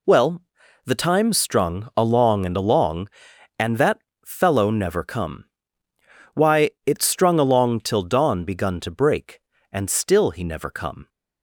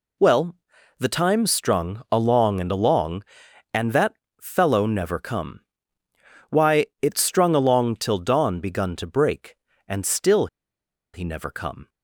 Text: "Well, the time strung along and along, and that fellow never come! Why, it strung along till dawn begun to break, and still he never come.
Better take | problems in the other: first | pauses between "that" and "fellow"; slight; at 4.1 s; 0.26 s long; slight in the first // pauses between "still" and "he"; noticeable; at 10.4 s; 0.67 s long

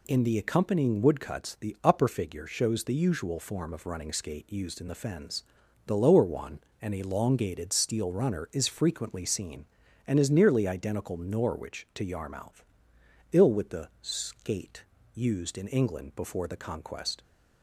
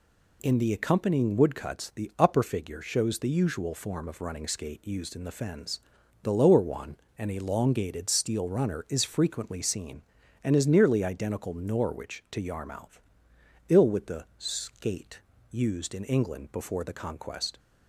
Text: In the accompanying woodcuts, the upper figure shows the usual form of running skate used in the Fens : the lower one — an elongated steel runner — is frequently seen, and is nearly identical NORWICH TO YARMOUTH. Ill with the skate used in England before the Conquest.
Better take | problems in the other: neither | pauses between "skate" and "used"; slight; the same in both

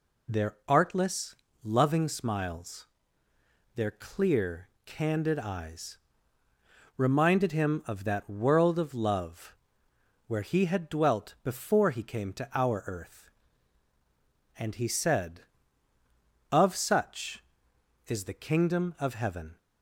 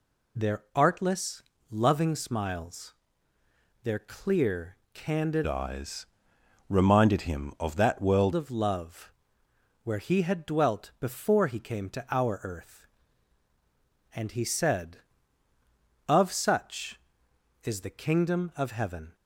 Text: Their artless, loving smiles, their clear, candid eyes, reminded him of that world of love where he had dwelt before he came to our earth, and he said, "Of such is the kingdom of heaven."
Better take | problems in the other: first | changes voice from "eyes" to "world"; from 5.4 to 8.3 s; 2.9 s long // pauses between "love" and "where"; noticeable; at 9.1 s; 0.70 s long; noticeable in the first

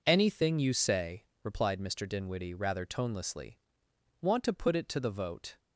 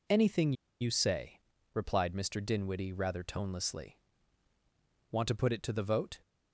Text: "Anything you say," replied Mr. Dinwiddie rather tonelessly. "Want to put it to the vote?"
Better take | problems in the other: first | pauses between "Anything" and "you"; slight; at 0.5 s; 0.27 s long

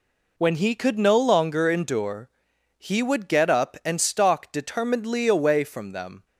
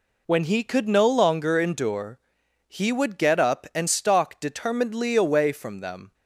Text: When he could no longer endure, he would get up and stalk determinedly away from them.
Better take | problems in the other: neither | none

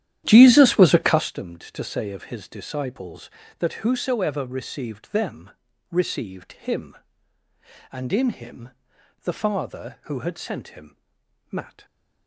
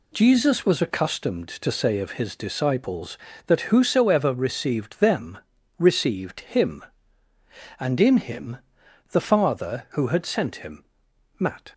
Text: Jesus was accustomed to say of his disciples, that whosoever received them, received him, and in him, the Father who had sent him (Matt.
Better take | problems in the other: second | starts louder than the rest; strong; until 1.3 s; 11.5 dB

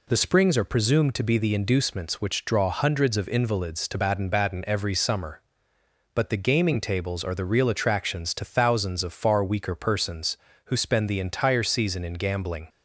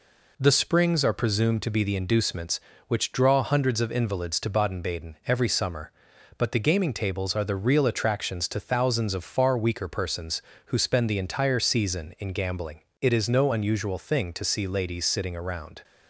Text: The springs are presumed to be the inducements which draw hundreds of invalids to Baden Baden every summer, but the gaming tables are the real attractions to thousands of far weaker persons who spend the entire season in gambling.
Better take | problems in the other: first | goes on to say "It is no unusual thing to see ladies sitting around"; strong; from 13.0 s on; 2.8 s long

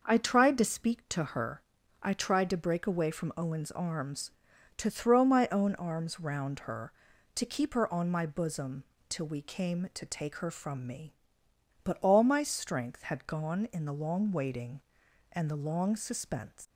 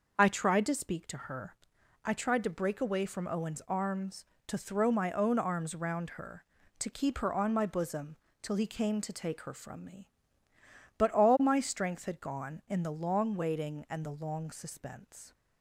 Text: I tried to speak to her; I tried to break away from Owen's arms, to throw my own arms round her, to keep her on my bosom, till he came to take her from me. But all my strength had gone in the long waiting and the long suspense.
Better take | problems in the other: second | starts louder than the rest; noticeable; until 1.0 s; 6 dB; also in the second // says "we" for "he"; at 9.2 s

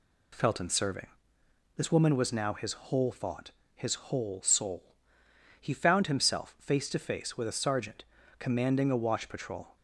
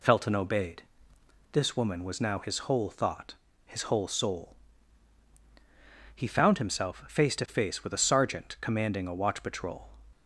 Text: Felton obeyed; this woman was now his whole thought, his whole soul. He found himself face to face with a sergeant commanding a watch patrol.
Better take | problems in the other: second | says "serving" for "obeyed"; at 0.6 s // pauses between "sergeant" and "commanding"; slight; at 8.0 s; 0.32 s long

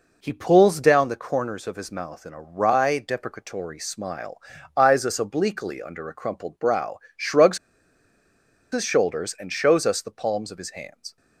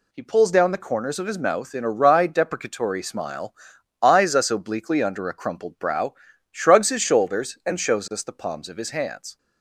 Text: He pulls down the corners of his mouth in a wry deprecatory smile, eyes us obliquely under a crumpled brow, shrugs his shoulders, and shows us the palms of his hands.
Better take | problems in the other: second | pauses between "shrugs" and "his"; at 7.5 s; 1.1 s long

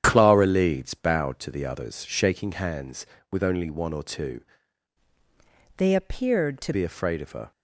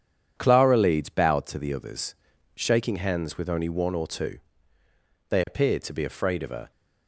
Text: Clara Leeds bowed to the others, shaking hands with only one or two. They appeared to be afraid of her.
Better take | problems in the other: second | starts louder than the rest; strong; until 1.0 s; 9 dB // changes voice from "They" to "to"; from 5.7 to 6.7 s; 1.0 s long

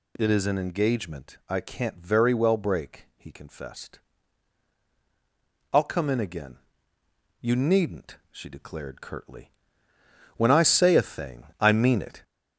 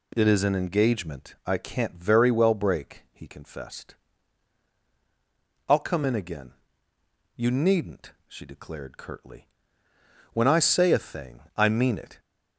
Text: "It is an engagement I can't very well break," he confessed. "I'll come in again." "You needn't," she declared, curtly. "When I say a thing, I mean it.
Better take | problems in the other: second | gets louder; slight; throughout; 2.5 dB

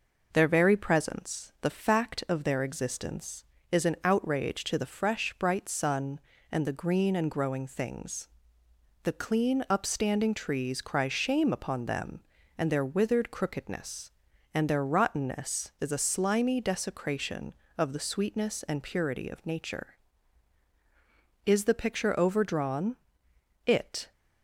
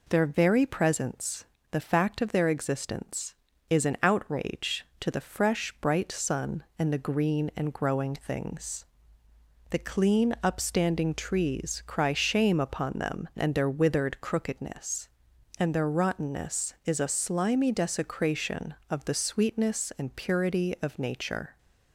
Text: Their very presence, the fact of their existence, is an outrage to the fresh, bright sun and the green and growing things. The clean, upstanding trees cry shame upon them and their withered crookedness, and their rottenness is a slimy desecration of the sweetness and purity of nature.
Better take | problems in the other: second | goes on to say "Is the picture overdrawn It"; strong; from 21.4 s on; 2.6 s long

